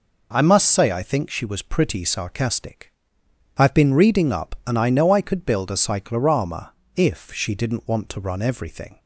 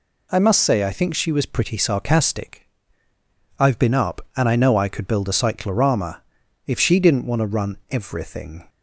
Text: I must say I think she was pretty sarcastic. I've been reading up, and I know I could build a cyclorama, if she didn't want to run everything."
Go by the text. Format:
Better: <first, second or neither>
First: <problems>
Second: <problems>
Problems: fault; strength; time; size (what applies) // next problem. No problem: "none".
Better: first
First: none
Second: skips "reading"; at 3.9 s